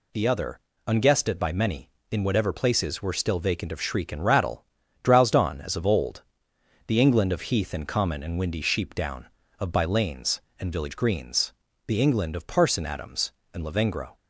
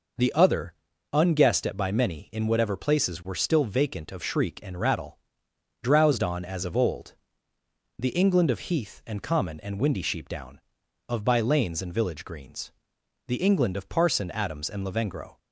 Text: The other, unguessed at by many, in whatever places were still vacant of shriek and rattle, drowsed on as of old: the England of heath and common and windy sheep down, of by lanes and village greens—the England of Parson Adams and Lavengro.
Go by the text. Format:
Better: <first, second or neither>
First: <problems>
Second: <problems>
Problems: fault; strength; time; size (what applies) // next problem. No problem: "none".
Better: neither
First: none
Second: none